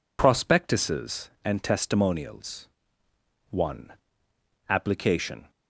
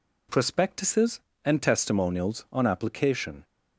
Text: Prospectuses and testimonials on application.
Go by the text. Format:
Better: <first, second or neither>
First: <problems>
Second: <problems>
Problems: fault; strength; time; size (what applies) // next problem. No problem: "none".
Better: second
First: says "one" for "on"; at 3.5 s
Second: none